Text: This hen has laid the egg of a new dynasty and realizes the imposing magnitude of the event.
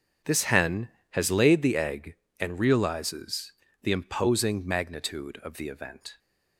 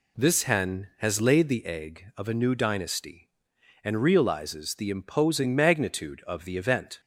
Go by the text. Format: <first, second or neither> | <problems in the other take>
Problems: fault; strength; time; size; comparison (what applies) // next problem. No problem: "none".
second | starts louder than the rest; until 1.4 s; 7 dB // skips "of a new dynasty"; at 2.2 s // pauses between "realizes" and "the"; slight; at 3.5 s; 0.30 s long